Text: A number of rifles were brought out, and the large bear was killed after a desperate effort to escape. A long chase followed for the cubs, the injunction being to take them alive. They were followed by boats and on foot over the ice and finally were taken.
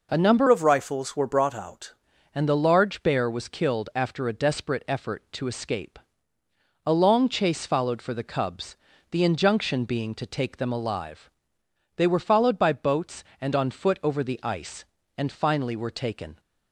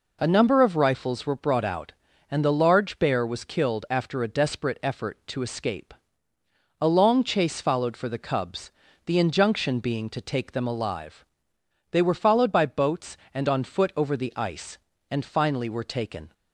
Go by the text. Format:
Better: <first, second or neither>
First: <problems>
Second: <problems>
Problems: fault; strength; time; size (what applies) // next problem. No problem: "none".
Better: second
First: changes voice from "of" to "out"; from 0.4 to 1.9 s; 1.5 s long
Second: none